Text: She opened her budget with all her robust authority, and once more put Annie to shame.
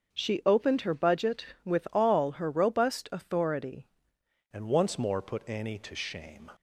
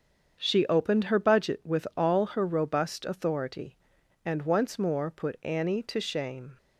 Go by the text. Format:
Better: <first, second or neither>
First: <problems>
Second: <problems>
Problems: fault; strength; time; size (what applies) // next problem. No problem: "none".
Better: second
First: starts louder than the rest; until 1.1 s; 6.5 dB // changes voice at "and"; from 4.5 s on; 2.0 s long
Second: starts louder than the rest; until 1.4 s; 7 dB